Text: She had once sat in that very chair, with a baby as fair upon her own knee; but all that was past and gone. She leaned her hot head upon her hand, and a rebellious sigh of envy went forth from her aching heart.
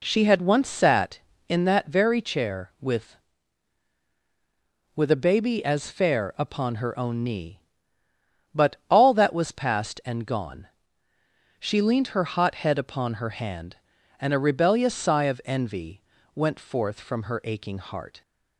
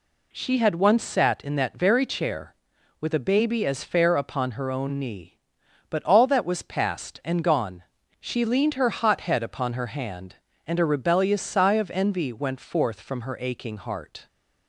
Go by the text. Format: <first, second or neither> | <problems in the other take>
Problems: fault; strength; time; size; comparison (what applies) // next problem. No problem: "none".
second | says "with" twice; at 4.9 s // pauses between "envy" and "went"; slight; at 16.0 s; 0.32 s long